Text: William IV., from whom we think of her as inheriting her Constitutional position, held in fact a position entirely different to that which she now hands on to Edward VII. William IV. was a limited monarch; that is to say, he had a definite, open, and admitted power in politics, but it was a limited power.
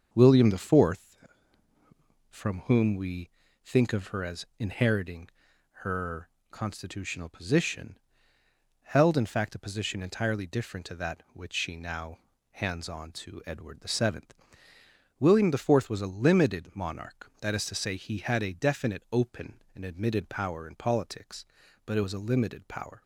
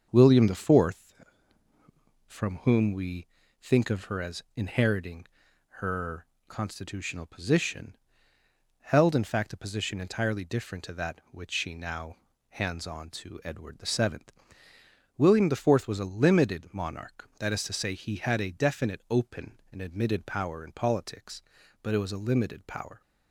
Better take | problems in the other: neither | starts louder than the rest; the same in both // pauses between "we" and "think"; slight; the same in both // pauses between "inheriting" and "her"; noticeable; the same in both // pauses between "her" and "Constitutional"; slight; the same in both // pauses between "now" and "hands"; slight; the same in both

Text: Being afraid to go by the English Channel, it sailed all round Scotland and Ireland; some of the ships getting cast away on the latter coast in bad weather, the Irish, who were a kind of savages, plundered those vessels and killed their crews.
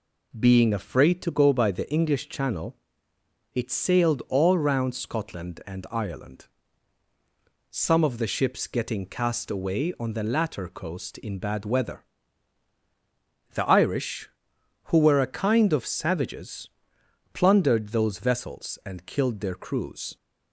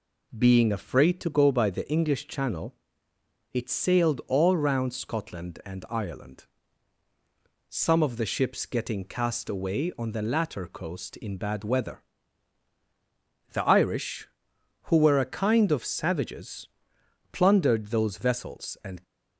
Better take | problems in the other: first | stops before "killed their crews"; at 19.0 s

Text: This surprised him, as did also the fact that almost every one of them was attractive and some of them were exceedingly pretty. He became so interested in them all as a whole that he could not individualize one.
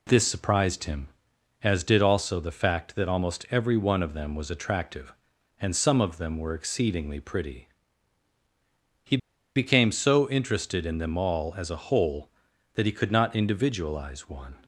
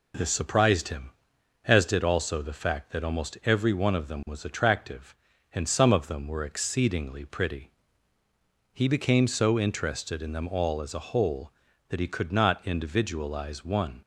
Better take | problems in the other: second | pauses between "He" and "became"; at 9.1 s; 0.38 s long

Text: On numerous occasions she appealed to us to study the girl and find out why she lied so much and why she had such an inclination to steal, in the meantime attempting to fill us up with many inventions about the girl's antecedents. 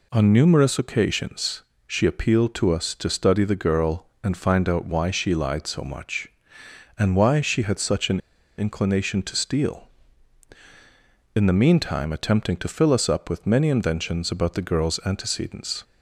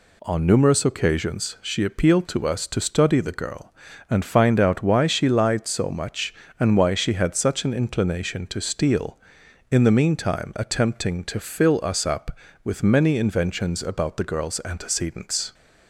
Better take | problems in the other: second | pauses between "occasions" and "she"; slight; at 1.6 s; 0.26 s long // pauses between "an" and "inclination"; at 8.1 s; 0.39 s long

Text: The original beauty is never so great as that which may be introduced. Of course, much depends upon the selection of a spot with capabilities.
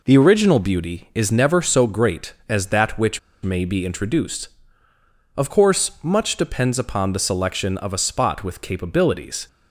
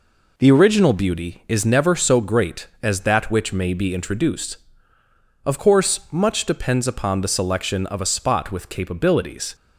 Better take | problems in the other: second | pauses between "which" and "may"; slight; at 3.1 s; 0.23 s long

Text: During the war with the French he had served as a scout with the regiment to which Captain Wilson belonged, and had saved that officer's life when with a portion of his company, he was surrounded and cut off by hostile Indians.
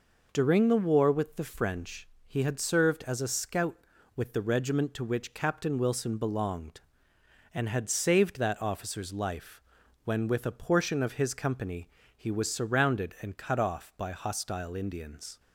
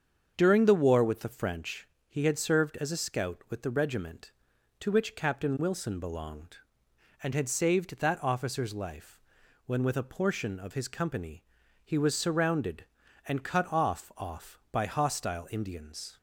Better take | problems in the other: first | starts louder than the rest; until 1.3 s; 7 dB // pauses between "French" and "he"; slight; at 1.8 s; 0.22 s long; slight in the first // pauses between "life" and "when"; noticeable; at 9.1 s; 0.48 s long; also in the first // says "off" twice; at 14.1 s

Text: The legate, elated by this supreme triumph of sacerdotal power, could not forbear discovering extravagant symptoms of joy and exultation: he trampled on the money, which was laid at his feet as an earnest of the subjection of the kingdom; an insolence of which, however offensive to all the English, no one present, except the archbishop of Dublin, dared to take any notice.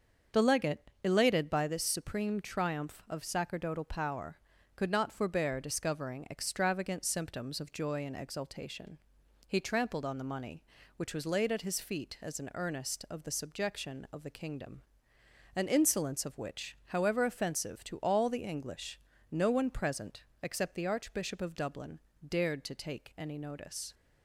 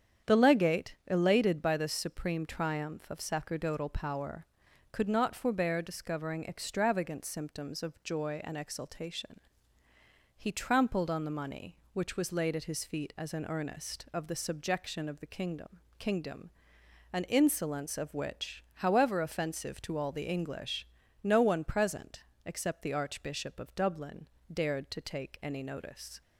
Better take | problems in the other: first | starts louder than the rest; strong; until 1.3 s; 8.5 dB; also in the first // says "kingdom" twice; at 15.9 s

